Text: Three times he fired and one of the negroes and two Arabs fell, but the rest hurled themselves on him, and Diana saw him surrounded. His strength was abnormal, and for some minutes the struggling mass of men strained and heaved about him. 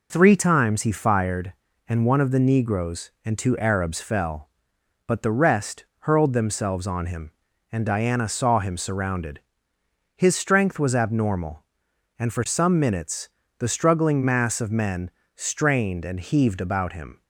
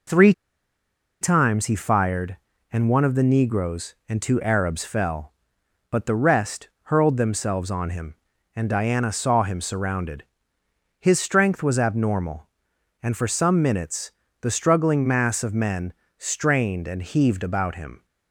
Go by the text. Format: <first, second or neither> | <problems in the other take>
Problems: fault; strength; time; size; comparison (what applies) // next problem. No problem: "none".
first | pauses between "Three" and "times"; noticeable; at 0.3 s; 0.88 s long // pauses between "minutes" and "the"; slight; at 14.1 s; 0.26 s long; slight in the first // pauses between "men" and "strained"; slight; at 15.9 s; 0.26 s long; slight in the first